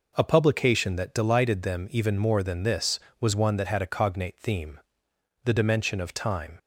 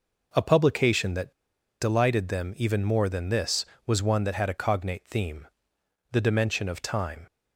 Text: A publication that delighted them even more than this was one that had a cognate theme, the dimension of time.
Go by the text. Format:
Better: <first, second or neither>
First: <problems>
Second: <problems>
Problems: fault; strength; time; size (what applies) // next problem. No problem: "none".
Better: first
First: none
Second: pauses between "that" and "delighted"; noticeable; at 1.3 s; 0.50 s long